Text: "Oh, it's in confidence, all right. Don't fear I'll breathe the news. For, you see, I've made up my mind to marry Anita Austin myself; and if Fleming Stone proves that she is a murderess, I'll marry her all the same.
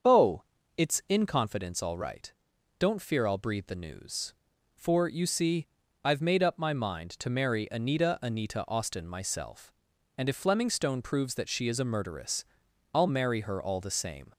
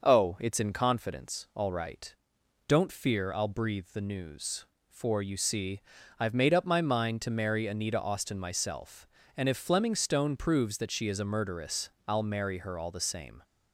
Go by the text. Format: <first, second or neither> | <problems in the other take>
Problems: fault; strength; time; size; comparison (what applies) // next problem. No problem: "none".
second | starts louder than the rest; until 1.4 s; 7 dB; noticeable in the second // says "Anita" twice; at 8.2 s